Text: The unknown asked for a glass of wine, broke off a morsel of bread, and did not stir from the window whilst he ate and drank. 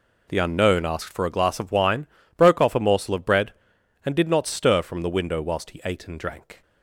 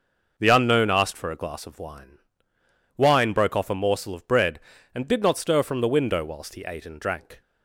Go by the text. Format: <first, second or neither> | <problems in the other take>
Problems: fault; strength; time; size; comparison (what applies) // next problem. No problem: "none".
first | says "wine" twice; at 2.9 s